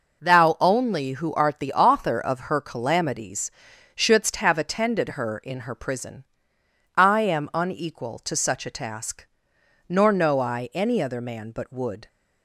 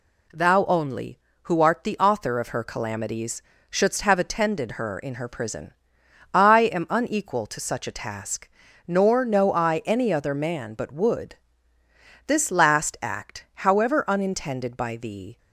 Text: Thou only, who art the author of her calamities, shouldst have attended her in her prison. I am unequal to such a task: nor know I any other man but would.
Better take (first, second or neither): first